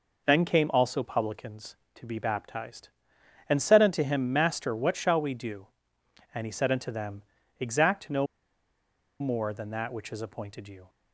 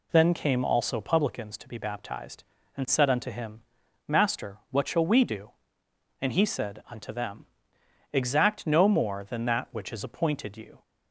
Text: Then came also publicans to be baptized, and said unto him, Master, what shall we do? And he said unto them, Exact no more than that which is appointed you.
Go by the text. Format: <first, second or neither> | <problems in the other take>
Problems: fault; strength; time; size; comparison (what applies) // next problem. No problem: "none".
second | pauses between "no" and "more"; noticeable; at 8.2 s; 0.95 s long